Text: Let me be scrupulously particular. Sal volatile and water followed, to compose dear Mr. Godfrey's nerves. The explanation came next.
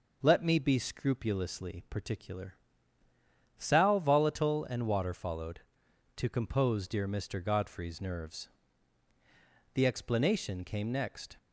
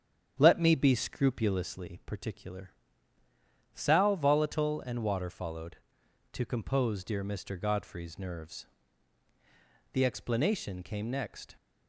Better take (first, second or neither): first